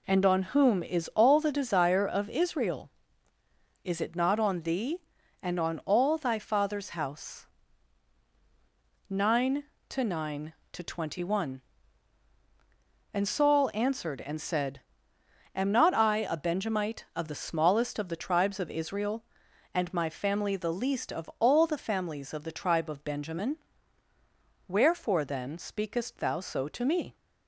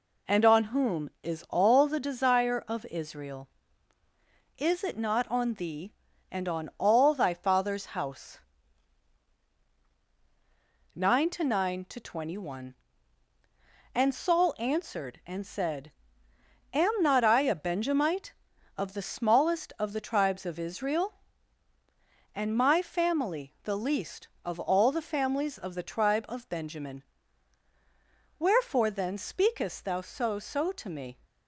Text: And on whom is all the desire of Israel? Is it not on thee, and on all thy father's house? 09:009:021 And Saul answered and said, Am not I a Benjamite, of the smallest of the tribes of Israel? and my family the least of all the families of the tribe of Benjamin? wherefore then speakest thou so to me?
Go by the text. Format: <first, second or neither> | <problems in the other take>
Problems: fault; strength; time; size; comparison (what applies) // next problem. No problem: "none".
first | says "so" twice; at 30.3 s